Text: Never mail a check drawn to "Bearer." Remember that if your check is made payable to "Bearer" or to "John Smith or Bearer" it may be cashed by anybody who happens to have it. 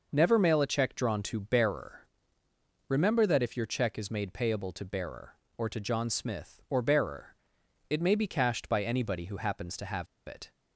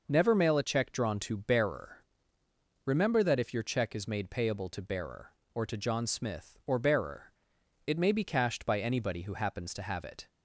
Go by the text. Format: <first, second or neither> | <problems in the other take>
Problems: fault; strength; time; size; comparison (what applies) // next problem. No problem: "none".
second | pauses between "Bearer" and "it"; noticeable; at 7.3 s; 0.56 s long; noticeable in the second // pauses between "have" and "it"; slight; at 10.0 s; 0.20 s long